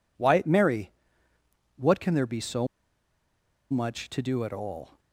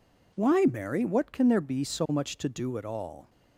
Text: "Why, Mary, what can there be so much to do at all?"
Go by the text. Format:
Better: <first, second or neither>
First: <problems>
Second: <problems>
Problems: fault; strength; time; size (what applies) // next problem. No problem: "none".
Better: second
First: pauses between "so" and "much"; at 2.6 s; 1.0 s long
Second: none